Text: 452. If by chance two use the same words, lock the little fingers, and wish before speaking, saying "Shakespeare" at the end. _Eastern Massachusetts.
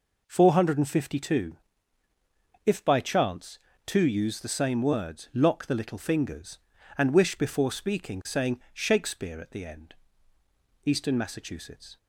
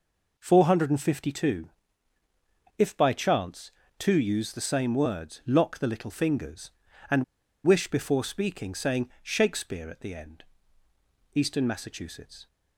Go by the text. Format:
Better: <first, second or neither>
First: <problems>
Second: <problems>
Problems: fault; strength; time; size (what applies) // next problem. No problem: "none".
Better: first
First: pauses between "chance" and "two"; slight; at 3.5 s; 0.28 s long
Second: pauses between "chance" and "two"; slight; at 3.7 s; 0.28 s long // pauses between "and" and "wish"; at 7.2 s; 0.40 s long